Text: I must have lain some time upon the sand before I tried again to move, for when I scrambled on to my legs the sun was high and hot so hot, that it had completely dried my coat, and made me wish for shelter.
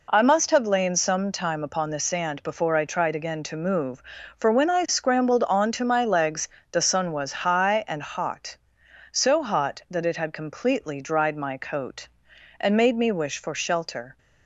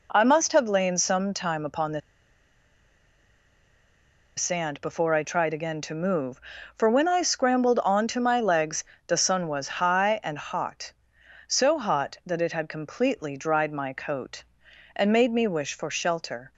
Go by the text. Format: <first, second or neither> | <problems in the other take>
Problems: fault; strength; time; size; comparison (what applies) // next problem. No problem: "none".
first | pauses between "the" and "sand"; strong; at 2.0 s; 2.3 s long // pauses between "legs" and "the"; slight; at 8.8 s; 0.20 s long; slight in the first